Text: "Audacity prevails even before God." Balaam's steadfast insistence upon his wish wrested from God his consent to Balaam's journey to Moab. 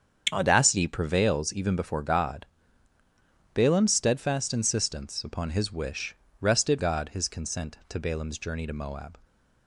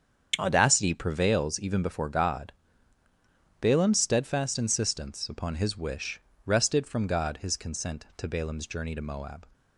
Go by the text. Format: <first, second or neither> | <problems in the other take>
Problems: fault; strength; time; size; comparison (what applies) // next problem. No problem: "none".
second | starts louder than the rest; strong; until 1.3 s; 7.5 dB; strong in the second // pauses between "wish" and "wrested"; slight; at 6.1 s; 0.26 s long; slight in the second // skips "from"; at 6.7 s